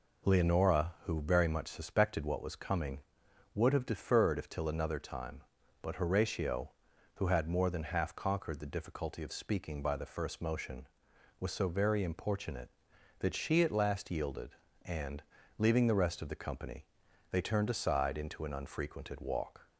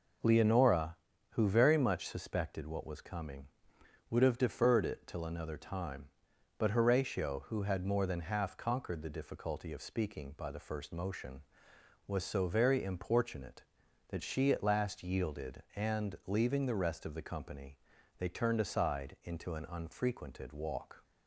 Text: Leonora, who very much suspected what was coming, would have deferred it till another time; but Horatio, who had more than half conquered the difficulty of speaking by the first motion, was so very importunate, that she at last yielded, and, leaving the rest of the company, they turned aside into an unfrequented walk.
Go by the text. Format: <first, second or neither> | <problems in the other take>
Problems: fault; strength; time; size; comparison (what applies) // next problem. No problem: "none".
second | says "if" for "it"; at 4.3 s